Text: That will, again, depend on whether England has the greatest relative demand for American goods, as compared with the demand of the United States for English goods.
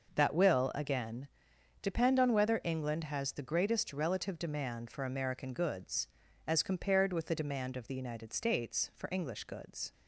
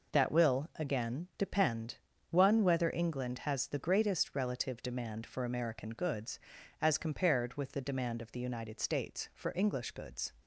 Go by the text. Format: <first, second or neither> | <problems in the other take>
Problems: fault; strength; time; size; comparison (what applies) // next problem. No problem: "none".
first | says "one" for "on"; at 2.3 s